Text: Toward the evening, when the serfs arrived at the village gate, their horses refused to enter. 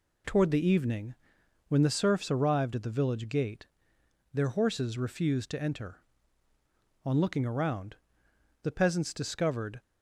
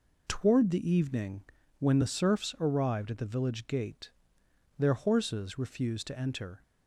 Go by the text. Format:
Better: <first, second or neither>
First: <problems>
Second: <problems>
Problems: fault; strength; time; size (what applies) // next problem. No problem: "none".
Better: second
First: goes on to say "On looking around the peasants discovered"; strong; from 7.0 s on; 2.7 s long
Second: none